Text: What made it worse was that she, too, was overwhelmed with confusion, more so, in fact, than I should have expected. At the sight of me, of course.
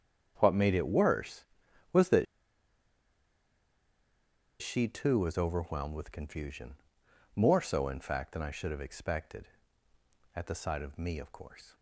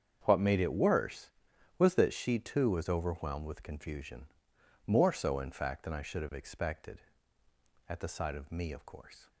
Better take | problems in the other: second | starts louder than the rest; strong; until 1.3 s; 7.5 dB; strong in the second // pauses between "that" and "she"; strong; at 2.2 s; 2.3 s long

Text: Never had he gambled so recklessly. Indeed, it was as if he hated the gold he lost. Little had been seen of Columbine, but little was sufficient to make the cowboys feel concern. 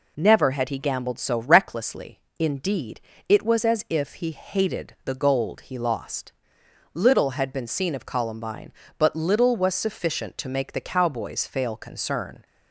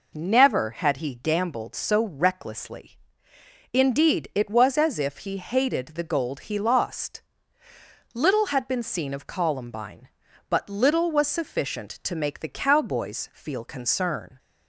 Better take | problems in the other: second | says "fail" for "feel"; at 11.4 s

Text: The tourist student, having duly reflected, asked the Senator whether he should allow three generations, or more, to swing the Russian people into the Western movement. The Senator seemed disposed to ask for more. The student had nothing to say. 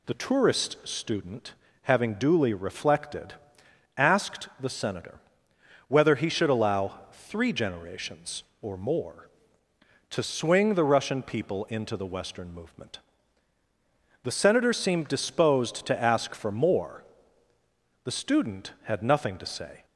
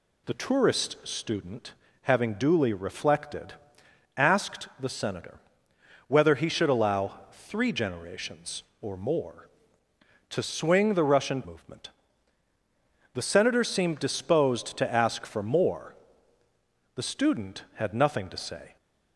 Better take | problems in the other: first | pauses between "Senator" and "whether"; noticeable; at 5.3 s; 0.68 s long; noticeable in the first // skips "people into the Western"; at 11.4 s

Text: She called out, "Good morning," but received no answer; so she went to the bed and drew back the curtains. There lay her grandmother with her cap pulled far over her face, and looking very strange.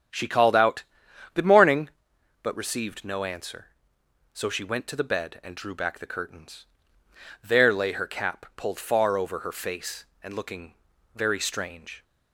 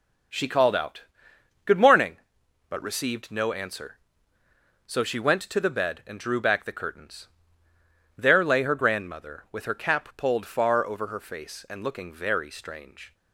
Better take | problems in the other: second | starts louder than the rest; strong; until 1.6 s; 8.5 dB; also in the second // skips "her grandmother with"; at 7.9 s // pauses between "looking" and "very"; at 10.7 s; 0.40 s long

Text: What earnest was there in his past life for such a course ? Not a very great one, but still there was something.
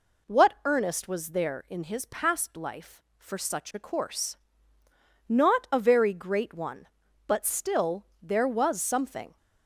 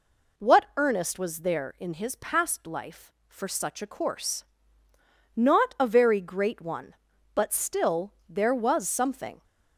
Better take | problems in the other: neither | none

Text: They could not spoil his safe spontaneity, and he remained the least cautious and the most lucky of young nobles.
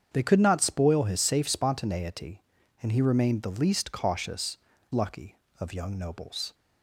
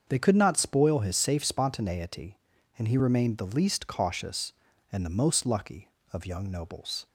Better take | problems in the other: second | starts louder than the rest; strong; until 1.1 s; 7.5 dB; also in the second // skips "and the most"; at 4.7 s

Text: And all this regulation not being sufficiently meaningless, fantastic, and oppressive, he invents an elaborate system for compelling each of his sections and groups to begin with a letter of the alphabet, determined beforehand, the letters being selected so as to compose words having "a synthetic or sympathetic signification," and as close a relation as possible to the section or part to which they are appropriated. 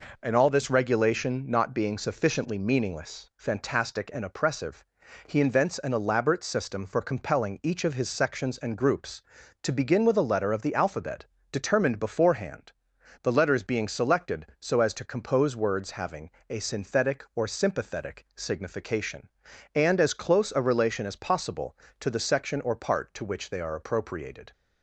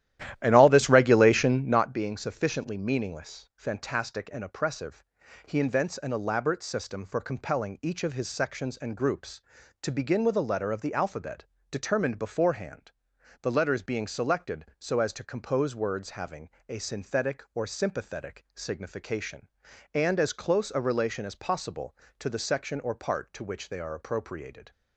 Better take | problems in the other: first | starts louder than the rest; strong; until 2.0 s; 13 dB // pauses between "having" and "a"; slight; at 16.5 s; 0.18 s long; slight in the first

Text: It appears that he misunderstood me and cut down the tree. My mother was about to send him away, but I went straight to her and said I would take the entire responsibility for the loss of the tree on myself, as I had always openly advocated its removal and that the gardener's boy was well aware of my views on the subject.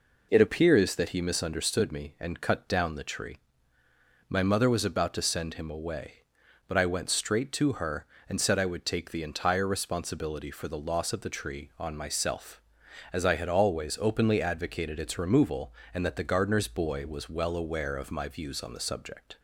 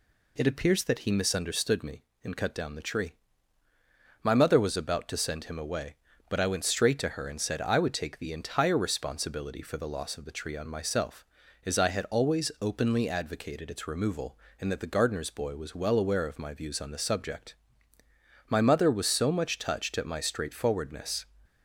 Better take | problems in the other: first | goes on to say "My mother was so much touched at my straightforwardness"; strong; from 18.4 s on; 2.8 s long

